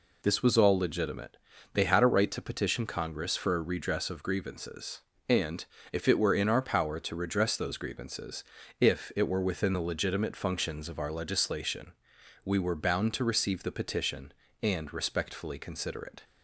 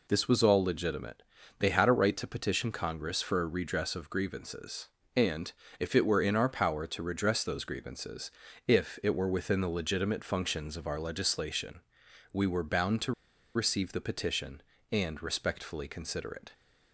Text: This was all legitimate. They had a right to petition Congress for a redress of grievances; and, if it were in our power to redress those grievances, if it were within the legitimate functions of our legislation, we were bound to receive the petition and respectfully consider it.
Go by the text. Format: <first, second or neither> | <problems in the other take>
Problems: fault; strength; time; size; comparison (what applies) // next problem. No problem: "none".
first | pauses between "to" and "receive"; at 13.1 s; 0.41 s long